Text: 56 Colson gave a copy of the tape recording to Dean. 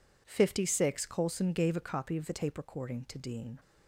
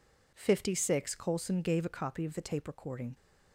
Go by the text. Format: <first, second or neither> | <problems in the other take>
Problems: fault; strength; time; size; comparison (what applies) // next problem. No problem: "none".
first | stops before "to Dean"; at 3.1 s